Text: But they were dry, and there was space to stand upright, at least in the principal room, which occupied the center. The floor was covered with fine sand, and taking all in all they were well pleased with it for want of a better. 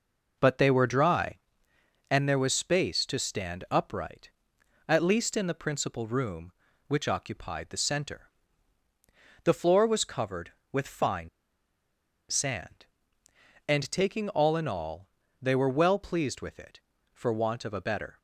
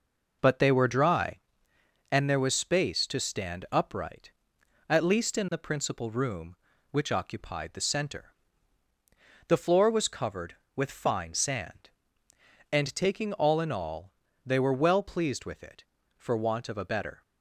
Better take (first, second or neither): second